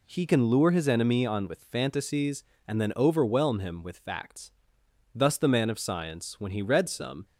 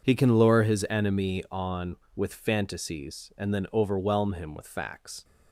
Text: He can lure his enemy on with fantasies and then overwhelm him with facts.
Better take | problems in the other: second | goes on to say "Thus the man of science when he read some"; strong; from 5.1 s on; 2.1 s long

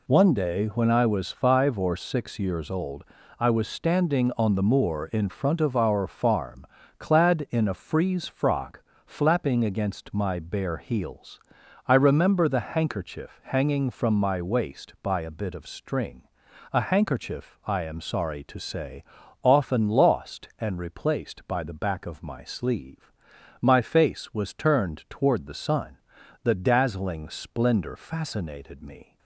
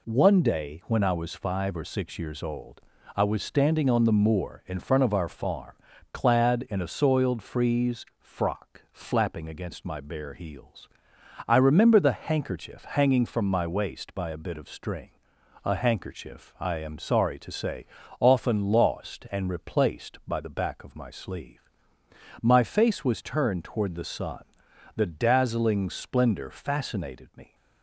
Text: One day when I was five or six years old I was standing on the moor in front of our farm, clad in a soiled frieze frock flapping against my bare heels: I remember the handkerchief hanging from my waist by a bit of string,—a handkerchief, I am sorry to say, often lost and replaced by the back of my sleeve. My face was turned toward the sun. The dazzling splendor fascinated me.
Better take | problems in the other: second | pauses between "old" and "I"; slight; at 3.0 s; 0.34 s long; slight in the second // skips "soiled"; at 7.7 s // pauses between "frock" and "flapping"; slight; at 8.8 s; 0.24 s long

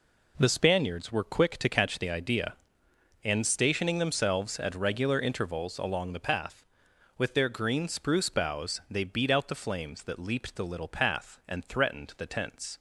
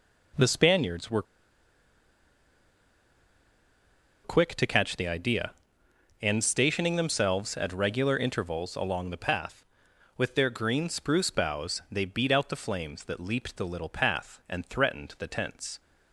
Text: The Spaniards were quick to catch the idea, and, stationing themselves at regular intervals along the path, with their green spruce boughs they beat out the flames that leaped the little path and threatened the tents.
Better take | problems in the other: first | pauses between "were" and "quick"; strong; at 1.2 s; 3.0 s long

